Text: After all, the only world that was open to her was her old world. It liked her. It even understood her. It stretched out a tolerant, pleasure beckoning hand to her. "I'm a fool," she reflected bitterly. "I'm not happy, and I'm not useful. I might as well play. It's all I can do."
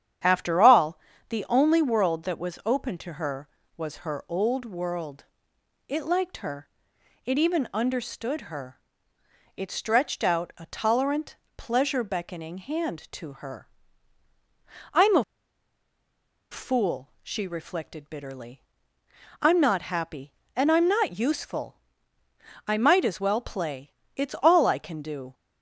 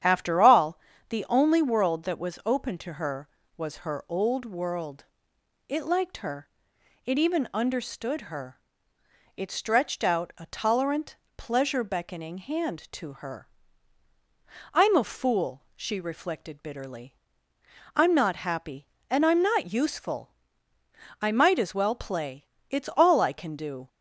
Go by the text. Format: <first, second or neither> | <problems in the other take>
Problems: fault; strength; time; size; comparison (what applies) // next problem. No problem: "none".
second | starts louder than the rest; strong; until 1.5 s; 9 dB; strong in the second // pauses between "a" and "fool"; strong; at 15.2 s; 1.2 s long